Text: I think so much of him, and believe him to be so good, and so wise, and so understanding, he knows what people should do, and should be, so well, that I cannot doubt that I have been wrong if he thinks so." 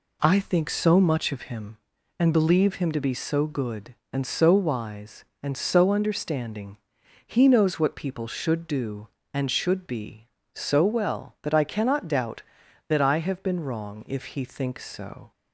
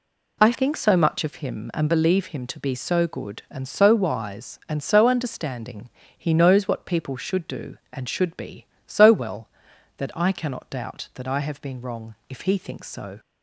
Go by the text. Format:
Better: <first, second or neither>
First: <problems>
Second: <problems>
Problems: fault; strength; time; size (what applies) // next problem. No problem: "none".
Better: first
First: none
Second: changes voice at "think"; from 0.5 s on; 12.6 s long // pauses between "wrong" and "if"; slight; at 12.1 s; 0.16 s long